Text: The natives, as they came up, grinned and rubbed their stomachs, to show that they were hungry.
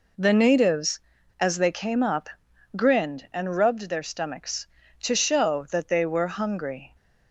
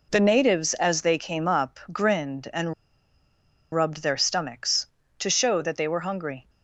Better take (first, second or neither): first